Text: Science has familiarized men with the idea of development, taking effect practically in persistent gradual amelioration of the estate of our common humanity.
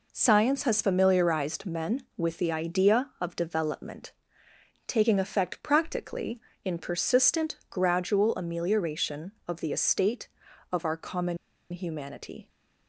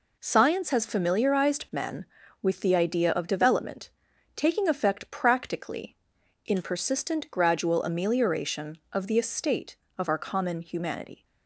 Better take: second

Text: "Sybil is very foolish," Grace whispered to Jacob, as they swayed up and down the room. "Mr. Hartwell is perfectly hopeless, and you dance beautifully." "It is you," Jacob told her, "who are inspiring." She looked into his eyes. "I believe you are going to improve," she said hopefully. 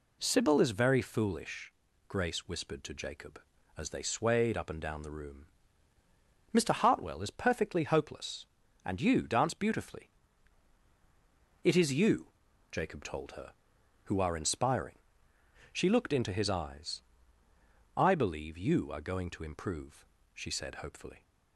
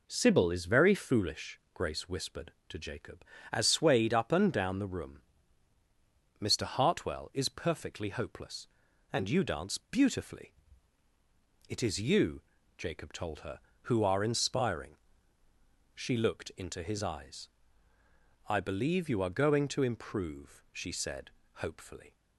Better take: first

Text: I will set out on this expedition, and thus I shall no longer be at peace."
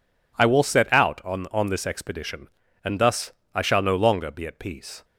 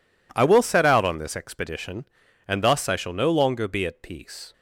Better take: second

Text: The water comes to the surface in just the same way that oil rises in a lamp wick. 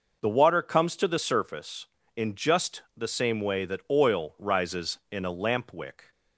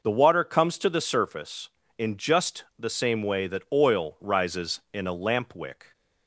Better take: neither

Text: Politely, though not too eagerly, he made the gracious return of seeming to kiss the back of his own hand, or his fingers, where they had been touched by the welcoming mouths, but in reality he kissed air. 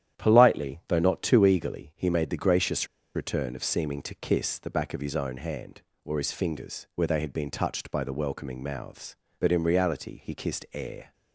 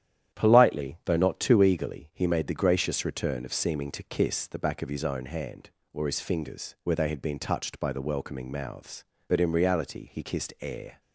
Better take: second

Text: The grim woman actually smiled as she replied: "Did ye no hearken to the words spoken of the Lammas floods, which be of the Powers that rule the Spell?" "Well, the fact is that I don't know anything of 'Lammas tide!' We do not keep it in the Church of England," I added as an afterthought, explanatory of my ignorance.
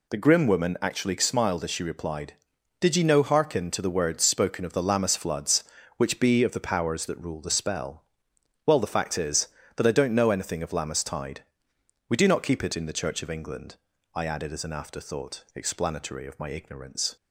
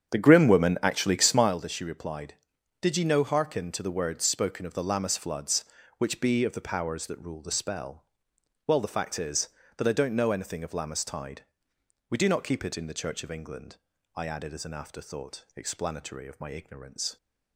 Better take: first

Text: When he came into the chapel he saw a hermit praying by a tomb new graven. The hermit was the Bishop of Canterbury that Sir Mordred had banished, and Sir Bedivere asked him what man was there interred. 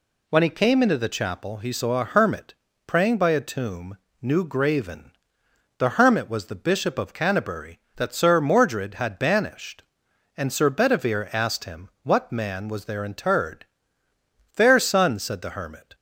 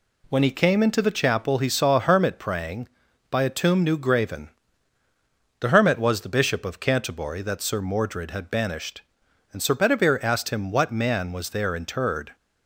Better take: second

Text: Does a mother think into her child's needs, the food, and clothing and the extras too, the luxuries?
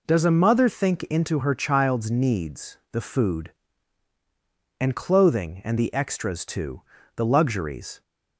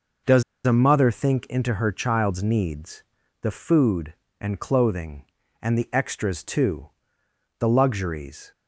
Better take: first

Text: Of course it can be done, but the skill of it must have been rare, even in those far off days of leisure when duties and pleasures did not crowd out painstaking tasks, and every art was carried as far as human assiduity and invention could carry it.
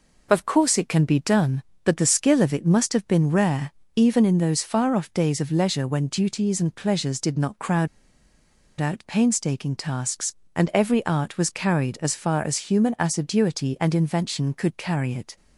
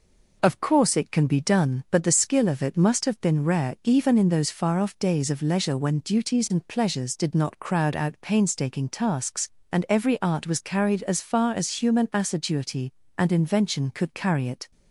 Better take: second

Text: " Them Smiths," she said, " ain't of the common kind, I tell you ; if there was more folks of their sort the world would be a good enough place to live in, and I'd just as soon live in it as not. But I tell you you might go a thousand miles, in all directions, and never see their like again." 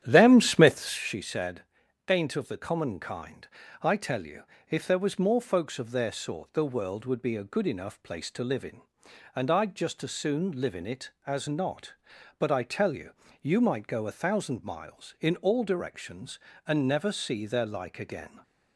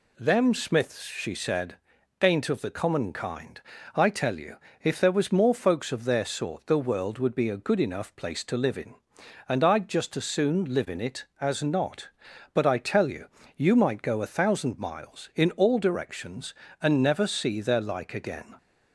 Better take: second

